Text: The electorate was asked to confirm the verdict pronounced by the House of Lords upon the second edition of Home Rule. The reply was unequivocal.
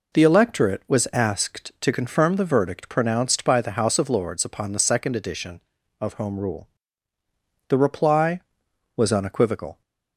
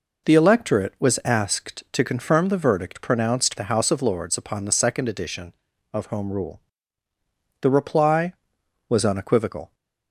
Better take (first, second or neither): first